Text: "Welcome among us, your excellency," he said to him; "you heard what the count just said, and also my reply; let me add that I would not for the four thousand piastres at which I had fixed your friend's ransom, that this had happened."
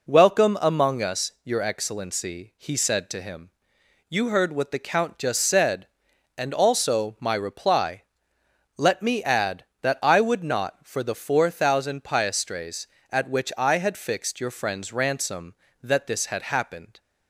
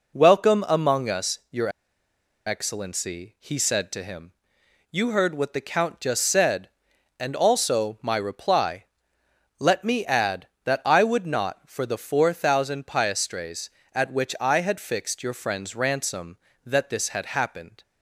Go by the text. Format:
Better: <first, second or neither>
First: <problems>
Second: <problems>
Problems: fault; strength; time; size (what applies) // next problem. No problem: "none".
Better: first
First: none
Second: pauses between "your" and "excellency"; noticeable; at 1.6 s; 0.77 s long